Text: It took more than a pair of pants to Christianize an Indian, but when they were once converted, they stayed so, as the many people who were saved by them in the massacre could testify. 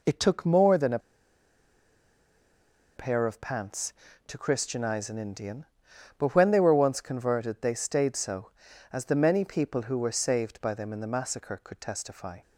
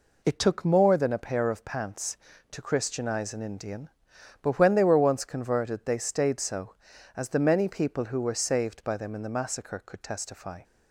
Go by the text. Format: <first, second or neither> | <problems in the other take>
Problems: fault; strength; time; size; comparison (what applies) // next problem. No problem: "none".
second | pauses between "a" and "pair"; strong; at 0.9 s; 1.9 s long